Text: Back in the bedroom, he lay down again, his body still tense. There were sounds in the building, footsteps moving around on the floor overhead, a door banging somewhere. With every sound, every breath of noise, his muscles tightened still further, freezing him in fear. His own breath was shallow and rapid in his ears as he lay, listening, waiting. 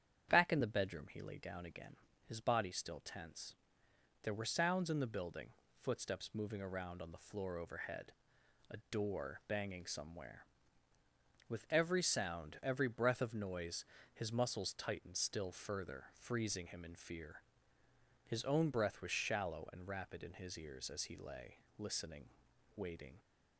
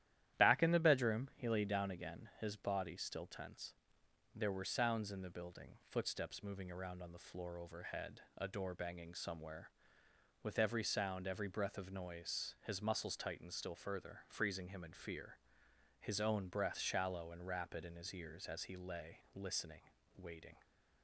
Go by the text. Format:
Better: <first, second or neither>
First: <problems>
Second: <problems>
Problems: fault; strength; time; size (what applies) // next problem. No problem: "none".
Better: first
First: starts louder than the rest; strong; until 1.3 s; 8.5 dB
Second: starts louder than the rest; strong; until 1.4 s; 12 dB // skips "was"; at 16.7 s